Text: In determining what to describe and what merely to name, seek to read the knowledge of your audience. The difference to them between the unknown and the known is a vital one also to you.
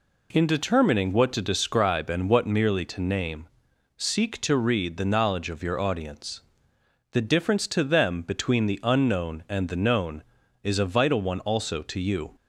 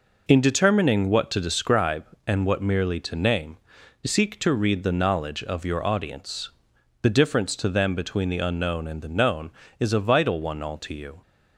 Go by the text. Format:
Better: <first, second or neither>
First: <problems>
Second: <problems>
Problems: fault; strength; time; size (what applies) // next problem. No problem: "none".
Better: first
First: none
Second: says "all" for "also"; at 10.6 s